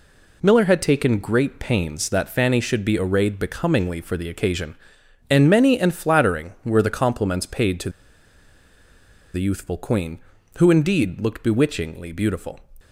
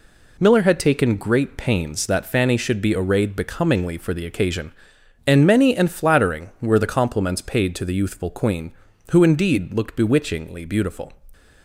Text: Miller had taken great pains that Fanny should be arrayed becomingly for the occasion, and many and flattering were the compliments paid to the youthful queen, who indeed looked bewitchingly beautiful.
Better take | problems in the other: second | pauses between "to" and "the"; strong; at 7.8 s; 1.4 s long

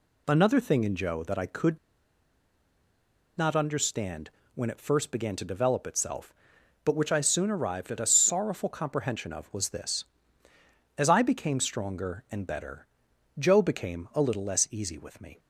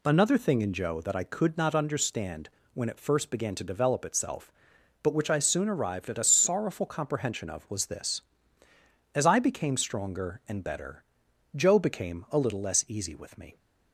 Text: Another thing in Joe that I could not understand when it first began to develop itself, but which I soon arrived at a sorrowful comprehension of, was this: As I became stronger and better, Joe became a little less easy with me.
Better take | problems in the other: second | pauses between "could" and "not"; strong; at 1.7 s; 1.6 s long // pauses between "understand" and "when"; slight; at 4.2 s; 0.24 s long; slight in the second

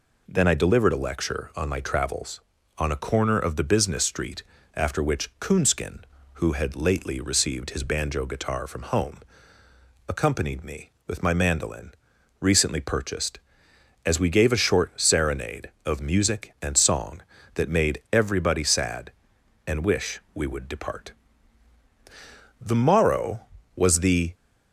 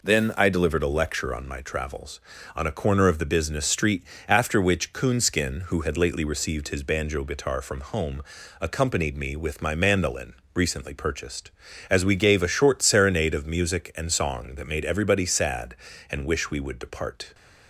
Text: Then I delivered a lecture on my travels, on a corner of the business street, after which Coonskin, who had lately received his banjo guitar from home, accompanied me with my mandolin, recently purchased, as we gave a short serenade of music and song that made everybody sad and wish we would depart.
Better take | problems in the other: second | goes on to say "The morrow was the"; strong; from 22.5 s on; 1.7 s long

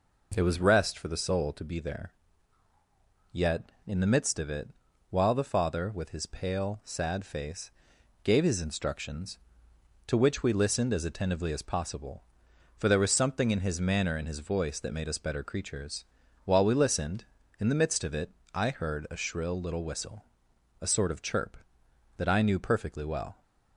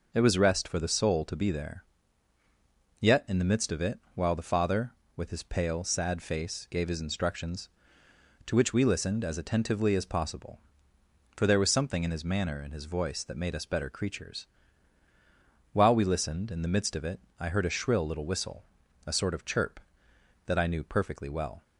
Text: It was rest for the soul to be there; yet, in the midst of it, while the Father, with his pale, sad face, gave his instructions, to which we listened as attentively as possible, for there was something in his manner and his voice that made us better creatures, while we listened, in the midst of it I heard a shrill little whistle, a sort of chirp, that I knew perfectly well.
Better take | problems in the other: neither | pauses between "it" and "I"; slight; the same in both

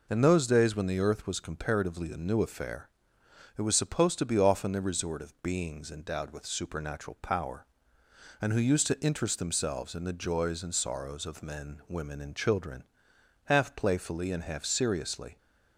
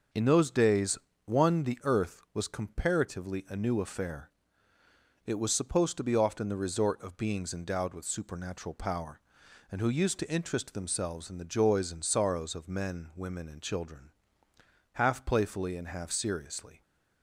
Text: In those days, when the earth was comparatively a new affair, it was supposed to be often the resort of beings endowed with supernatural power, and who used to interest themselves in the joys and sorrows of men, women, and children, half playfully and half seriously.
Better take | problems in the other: first | says "one" for "when"; at 1.2 s

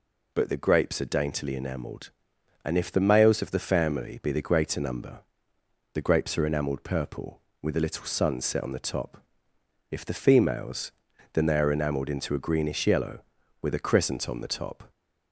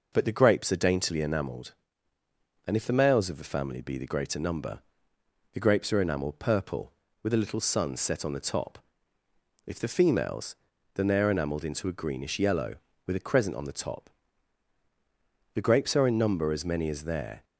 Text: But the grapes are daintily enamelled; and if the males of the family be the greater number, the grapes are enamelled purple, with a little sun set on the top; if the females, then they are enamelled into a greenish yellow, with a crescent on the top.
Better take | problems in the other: first | goes on to say "The grapes are in number as many as there"; strong; from 15.5 s on; 1.9 s long

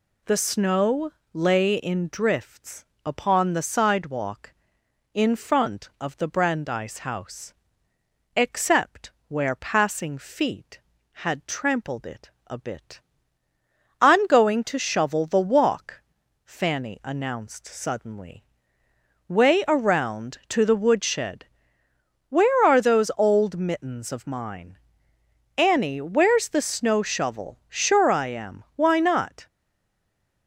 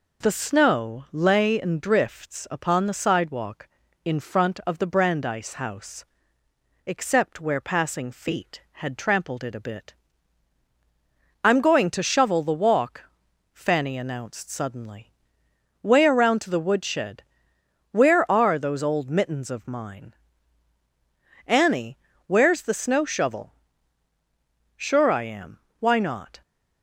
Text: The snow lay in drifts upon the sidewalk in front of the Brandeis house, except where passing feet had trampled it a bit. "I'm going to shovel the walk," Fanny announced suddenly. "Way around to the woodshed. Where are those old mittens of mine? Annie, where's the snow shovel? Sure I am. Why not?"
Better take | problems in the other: second | pauses between "snow" and "lay"; slight; at 1.1 s; 0.22 s long // pauses between "drifts" and "upon"; slight; at 2.8 s; 0.20 s long // pauses between "except" and "where"; slight; at 9.1 s; 0.16 s long // pauses between "it" and "a"; slight; at 12.3 s; 0.16 s long // stays silent after the last word; from 29.4 s on; 1.0 s long

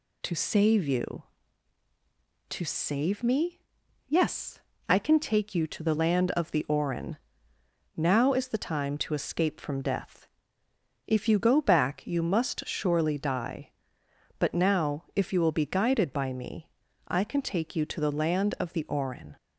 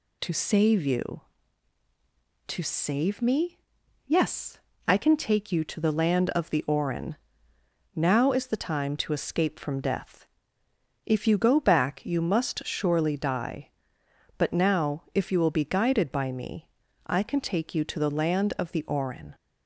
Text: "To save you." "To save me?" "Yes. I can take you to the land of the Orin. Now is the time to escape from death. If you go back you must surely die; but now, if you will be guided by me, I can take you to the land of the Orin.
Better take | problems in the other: neither | none

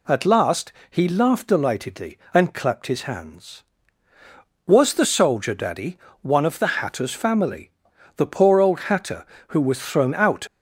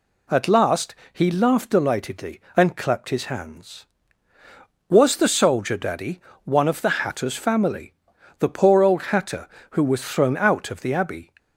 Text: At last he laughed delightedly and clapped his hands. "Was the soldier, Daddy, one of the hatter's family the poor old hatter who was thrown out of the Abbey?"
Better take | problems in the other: second | pauses between "last" and "he"; slight; at 0.7 s; 0.18 s long; slight in the second // pauses between "family" and "the"; noticeable; at 7.6 s; 0.46 s long; noticeable in the second // stops before "of the Abbey"; at 10.4 s

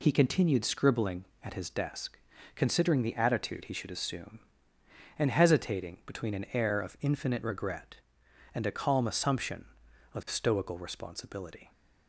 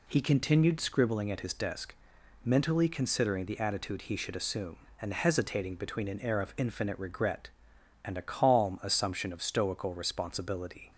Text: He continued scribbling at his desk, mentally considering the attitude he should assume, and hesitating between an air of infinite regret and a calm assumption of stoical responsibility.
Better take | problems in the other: second | skips "mentally"; at 2.3 s

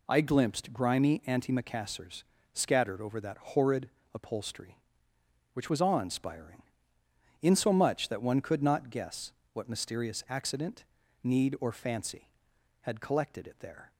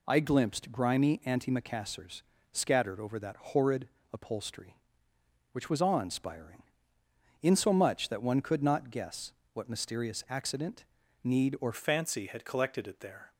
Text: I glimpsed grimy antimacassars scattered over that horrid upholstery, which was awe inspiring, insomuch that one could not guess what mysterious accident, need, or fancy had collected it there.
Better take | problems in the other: first | pauses between "antimacassars" and "scattered"; slight; at 2.2 s; 0.32 s long; slight in the first // pauses between "horrid" and "upholstery"; slight; at 3.8 s; 0.24 s long; slight in the first // pauses between "guess" and "what"; slight; at 9.3 s; 0.22 s long; slight in the first // changes voice at "fancy"; from 11.7 s on; 1.6 s long

